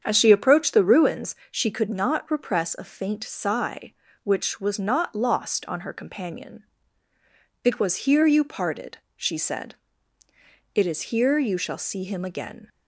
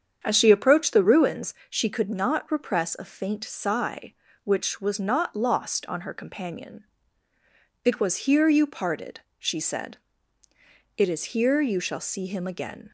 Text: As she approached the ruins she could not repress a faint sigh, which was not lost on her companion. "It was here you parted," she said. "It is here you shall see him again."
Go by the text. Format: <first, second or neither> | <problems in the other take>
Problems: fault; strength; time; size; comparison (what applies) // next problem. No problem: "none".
neither | starts louder than the rest; strong; the same in both // pauses between "ruins" and "she"; slight; the same in both